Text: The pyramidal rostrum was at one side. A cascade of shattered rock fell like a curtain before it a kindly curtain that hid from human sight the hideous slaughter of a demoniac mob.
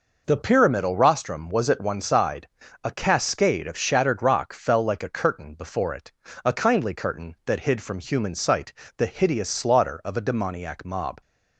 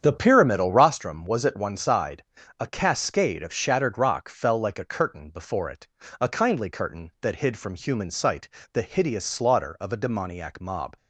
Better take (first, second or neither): first